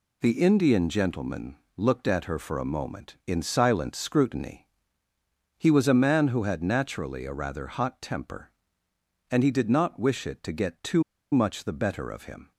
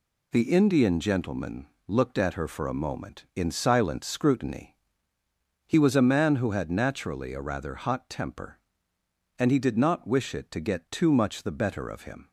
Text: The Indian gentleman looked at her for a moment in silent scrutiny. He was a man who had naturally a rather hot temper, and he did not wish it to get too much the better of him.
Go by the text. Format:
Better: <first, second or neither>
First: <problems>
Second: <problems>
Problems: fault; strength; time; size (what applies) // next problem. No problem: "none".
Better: second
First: pauses between "gentleman" and "looked"; slight; at 1.5 s; 0.20 s long // pauses between "too" and "much"; slight; at 11.0 s; 0.30 s long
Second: pauses between "gentleman" and "looked"; slight; at 1.6 s; 0.20 s long